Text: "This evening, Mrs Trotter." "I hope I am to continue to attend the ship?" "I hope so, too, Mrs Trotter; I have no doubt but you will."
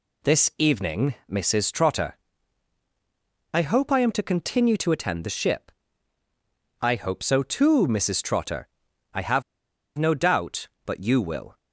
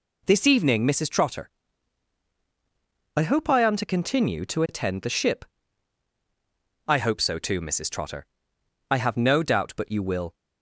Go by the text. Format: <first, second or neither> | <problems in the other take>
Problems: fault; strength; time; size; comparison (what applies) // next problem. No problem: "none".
second | pauses between "have" and "no"; noticeable; at 9.4 s; 0.55 s long